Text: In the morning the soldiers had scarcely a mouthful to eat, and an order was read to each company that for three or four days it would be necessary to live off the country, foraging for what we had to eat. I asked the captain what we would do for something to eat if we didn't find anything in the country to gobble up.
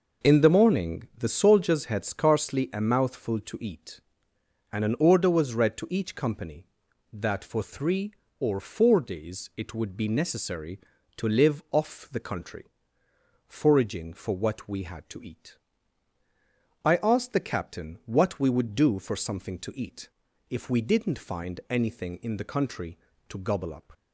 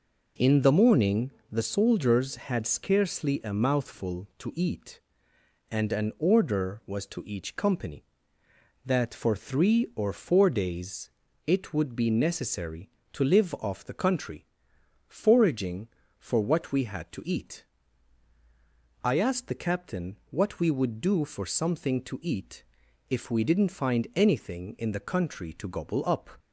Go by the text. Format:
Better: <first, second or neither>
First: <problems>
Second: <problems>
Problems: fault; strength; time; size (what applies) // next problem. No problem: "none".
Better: first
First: pauses between "eat" and "if"; at 20.0 s; 0.42 s long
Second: pauses between "morning" and "the"; slight; at 1.3 s; 0.20 s long // skips "read"; at 7.0 s // pauses between "days" and "it"; at 11.0 s; 0.38 s long // pauses between "eat" and "if"; noticeable; at 22.6 s; 0.46 s long